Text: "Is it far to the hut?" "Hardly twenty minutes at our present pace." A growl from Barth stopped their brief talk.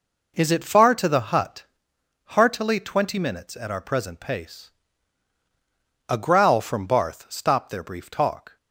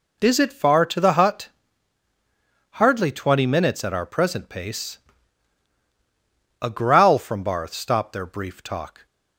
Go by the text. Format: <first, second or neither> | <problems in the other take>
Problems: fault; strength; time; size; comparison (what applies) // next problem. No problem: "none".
second | says "Heartily" for "Hardly"; at 2.2 s